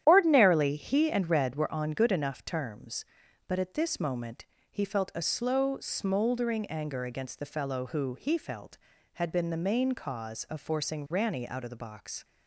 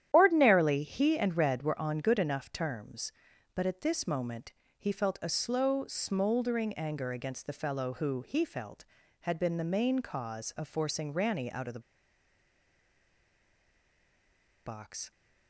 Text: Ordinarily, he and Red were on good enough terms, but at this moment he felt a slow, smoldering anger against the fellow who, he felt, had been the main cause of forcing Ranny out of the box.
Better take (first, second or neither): first